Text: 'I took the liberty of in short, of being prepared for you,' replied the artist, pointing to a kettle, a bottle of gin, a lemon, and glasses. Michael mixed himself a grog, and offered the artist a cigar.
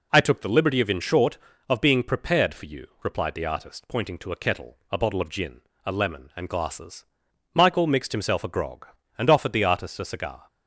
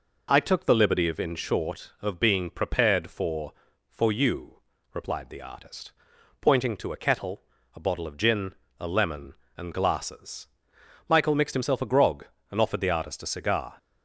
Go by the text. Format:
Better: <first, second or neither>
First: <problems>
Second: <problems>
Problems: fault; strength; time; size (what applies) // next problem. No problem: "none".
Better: first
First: none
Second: says "for" twice; at 3.8 s